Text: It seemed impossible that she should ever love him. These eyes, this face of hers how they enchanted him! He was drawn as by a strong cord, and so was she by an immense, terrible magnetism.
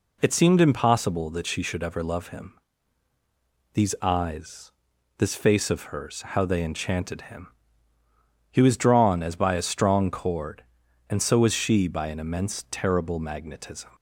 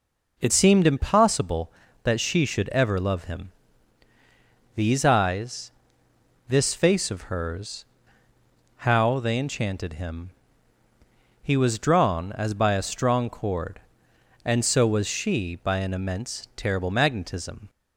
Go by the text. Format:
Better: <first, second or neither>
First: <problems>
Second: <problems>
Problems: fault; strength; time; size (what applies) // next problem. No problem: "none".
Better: first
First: none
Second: changes voice at "seemed"; from 0.5 s on; 17.1 s long // pauses between "hers" and "how"; noticeable; at 7.8 s; 0.96 s long